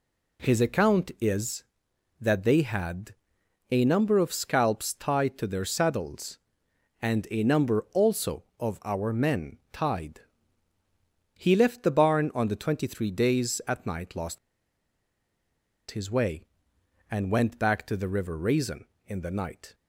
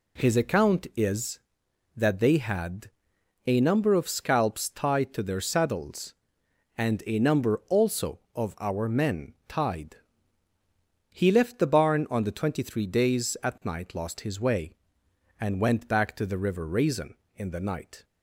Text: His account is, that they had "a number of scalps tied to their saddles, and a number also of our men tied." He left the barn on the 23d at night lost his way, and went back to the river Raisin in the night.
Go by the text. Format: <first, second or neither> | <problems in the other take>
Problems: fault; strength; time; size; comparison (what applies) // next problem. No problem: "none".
second | pauses between "had" and "a"; noticeable; at 3.1 s; 0.58 s long; noticeable in the second // pauses between "lost" and "his"; strong; at 14.3 s; 1.5 s long